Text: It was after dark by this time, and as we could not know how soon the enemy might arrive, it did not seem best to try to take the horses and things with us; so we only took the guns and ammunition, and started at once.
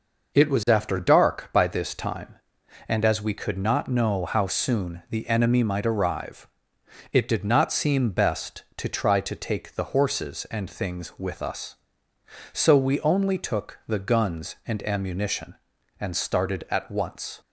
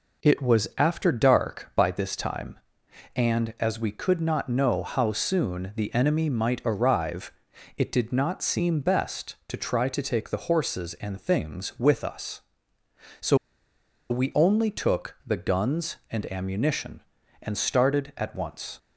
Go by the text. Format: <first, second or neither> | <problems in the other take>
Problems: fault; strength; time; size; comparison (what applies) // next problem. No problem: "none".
first | pauses between "so" and "we"; noticeable; at 13.3 s; 0.74 s long